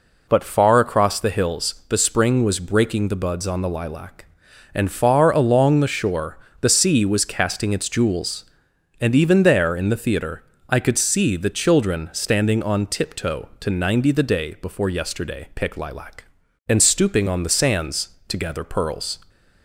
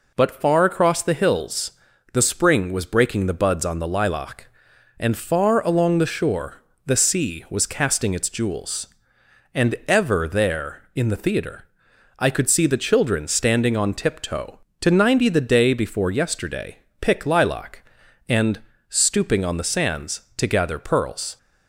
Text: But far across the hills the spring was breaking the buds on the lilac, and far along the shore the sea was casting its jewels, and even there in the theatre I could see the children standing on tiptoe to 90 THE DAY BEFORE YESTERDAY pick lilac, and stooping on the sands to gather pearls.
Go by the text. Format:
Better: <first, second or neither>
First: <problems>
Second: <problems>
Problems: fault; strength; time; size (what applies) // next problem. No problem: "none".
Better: first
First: pauses between "shore" and "the"; slight; at 6.3 s; 0.24 s long // pauses between "theatre" and "I"; slight; at 10.4 s; 0.26 s long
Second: pauses between "hills" and "the"; at 1.7 s; 0.42 s long // pauses between "shore" and "the"; slight; at 6.5 s; 0.30 s long // says "ever" for "even"; at 9.8 s // pauses between "theatre" and "I"; noticeable; at 11.6 s; 0.54 s long // pauses between "YESTERDAY" and "pick"; slight; at 16.7 s; 0.20 s long // pauses between "and" and "stooping"; slight; at 18.5 s; 0.30 s long